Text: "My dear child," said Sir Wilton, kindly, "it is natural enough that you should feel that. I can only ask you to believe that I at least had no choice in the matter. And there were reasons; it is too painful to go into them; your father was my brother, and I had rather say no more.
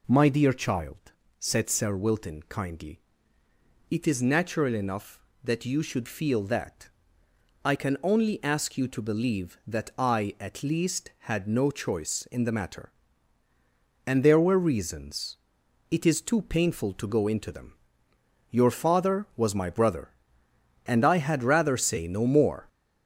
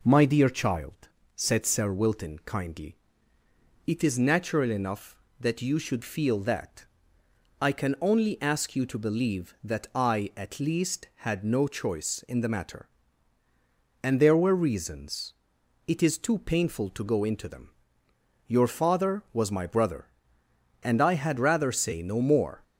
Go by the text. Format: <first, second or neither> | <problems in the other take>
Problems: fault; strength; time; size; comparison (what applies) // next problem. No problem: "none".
second | gets louder; noticeable; throughout; 5.5 dB